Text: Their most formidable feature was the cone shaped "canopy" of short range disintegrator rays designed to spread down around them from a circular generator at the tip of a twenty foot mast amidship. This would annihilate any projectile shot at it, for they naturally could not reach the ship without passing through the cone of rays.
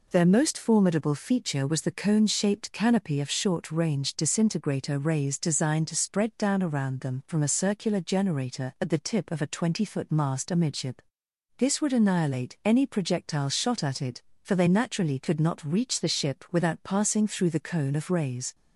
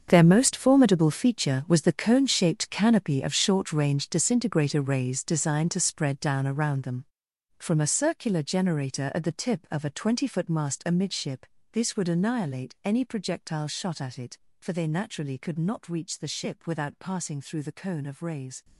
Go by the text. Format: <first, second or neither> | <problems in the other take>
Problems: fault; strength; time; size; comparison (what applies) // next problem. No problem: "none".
first | gets quieter; strong; throughout; 14.5 dB